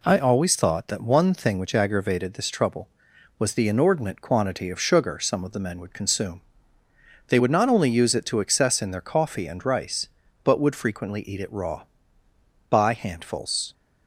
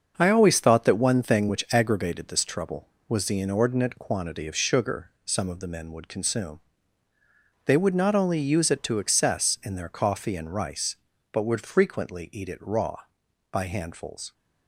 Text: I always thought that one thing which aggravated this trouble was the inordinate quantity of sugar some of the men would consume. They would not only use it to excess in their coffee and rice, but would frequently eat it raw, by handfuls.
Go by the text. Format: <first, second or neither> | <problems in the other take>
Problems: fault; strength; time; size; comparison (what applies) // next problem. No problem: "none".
first | gets quieter; throughout; 6.5 dB // pauses between "sugar" and "some"; slight; at 5.0 s; 0.16 s long